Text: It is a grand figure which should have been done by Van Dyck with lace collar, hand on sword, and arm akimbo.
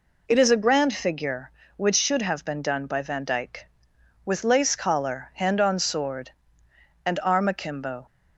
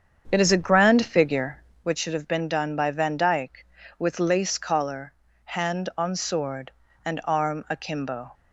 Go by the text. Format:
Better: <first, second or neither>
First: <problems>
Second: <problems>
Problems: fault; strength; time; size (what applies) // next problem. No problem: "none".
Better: first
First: none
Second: starts louder than the rest; strong; until 1.9 s; 7.5 dB